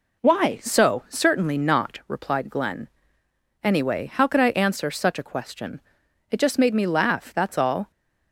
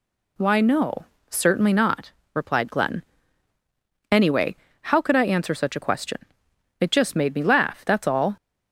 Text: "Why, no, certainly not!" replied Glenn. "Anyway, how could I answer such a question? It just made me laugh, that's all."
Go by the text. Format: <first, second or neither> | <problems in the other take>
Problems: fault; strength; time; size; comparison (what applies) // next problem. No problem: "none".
second | says "so" for "no"; at 0.5 s